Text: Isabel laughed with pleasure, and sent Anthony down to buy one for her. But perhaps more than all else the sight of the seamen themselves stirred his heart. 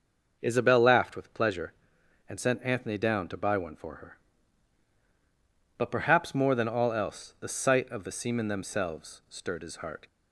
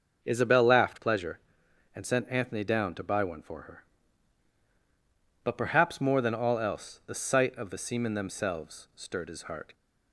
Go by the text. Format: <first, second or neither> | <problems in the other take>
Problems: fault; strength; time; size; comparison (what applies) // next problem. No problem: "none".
first | starts louder than the rest; until 1.2 s; 6.5 dB; also in the first // skips "with"; at 0.9 s